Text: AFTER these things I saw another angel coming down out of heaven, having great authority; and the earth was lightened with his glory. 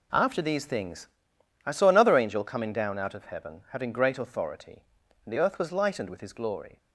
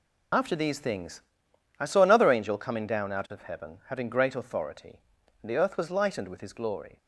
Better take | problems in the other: first | loses the start of "AFTER"; at 0.3 s; 65 ms // pauses between "things" and "I"; noticeable; at 1.2 s; 0.58 s long; noticeable in the first

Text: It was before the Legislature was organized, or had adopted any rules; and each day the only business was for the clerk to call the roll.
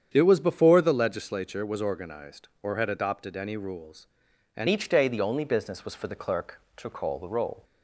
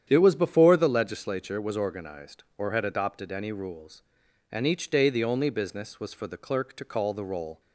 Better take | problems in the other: second | starts louder than the rest; strong; until 1.1 s; 8.5 dB; strong in the second // changes voice at "each"; from 4.6 s on; 3.0 s long

